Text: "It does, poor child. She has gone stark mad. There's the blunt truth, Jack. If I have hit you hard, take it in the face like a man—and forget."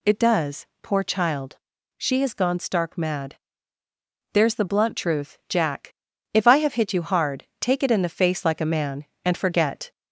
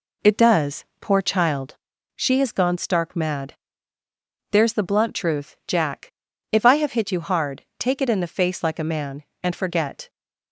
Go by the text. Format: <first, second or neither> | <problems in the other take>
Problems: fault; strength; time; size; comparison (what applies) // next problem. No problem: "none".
second | gets louder; slight; throughout; 2 dB